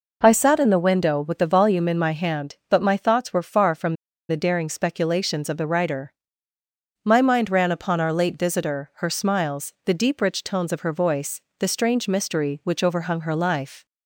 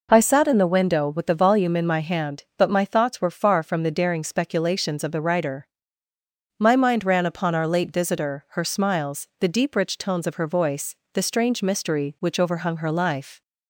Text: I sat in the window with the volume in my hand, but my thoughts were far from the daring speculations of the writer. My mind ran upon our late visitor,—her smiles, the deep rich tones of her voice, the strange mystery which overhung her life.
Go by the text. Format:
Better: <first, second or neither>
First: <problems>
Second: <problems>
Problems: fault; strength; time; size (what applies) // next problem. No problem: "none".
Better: second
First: pauses between "from" and "the"; slight; at 3.9 s; 0.33 s long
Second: none